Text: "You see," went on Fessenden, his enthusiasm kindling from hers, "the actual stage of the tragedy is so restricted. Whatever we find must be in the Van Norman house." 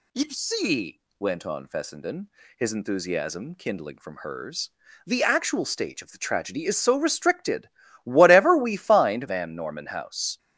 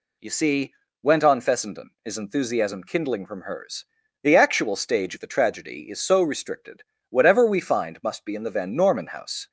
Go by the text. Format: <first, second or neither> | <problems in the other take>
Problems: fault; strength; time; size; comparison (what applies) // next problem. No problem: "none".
second | skips "must be in the"; at 9.2 s